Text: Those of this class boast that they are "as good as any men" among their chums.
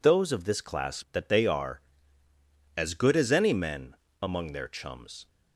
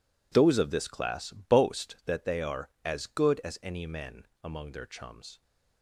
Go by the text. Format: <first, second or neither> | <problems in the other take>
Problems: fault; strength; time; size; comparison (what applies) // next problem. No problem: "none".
second | skips "boast"; at 1.0 s // pauses between "men" and "among"; slight; at 3.9 s; 0.26 s long; slight in the second